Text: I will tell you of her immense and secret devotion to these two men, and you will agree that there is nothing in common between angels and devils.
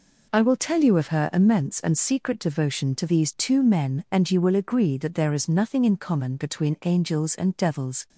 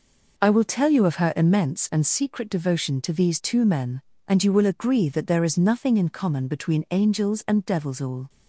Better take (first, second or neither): first